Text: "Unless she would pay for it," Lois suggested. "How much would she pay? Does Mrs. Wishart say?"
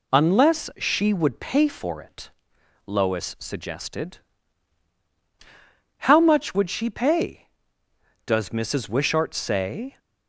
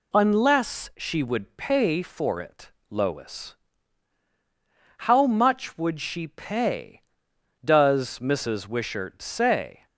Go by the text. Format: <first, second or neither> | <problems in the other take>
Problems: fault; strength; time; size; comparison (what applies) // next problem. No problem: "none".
first | skips "suggested"; at 4.2 s